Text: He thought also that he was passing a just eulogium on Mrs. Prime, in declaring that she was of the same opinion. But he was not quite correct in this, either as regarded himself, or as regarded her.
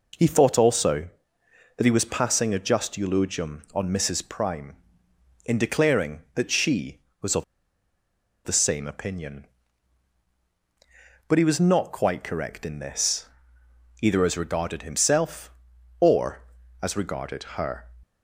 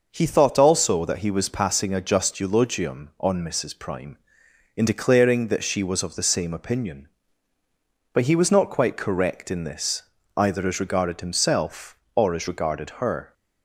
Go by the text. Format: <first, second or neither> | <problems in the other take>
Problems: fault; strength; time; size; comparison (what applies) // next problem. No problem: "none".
second | pauses between "of" and "the"; at 7.4 s; 1.0 s long